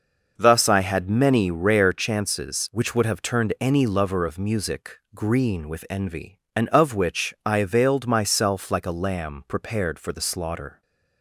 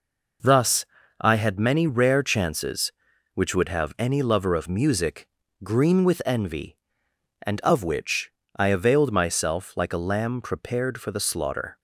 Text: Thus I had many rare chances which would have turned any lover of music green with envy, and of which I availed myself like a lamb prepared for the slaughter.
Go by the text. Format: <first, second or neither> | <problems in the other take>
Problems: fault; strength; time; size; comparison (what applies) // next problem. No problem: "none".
first | pauses between "Thus" and "I"; slight; at 0.8 s; 0.36 s long // skips "turned"; at 3.9 s // pauses between "music" and "green"; slight; at 5.2 s; 0.34 s long // pauses between "which" and "I"; slight; at 8.3 s; 0.24 s long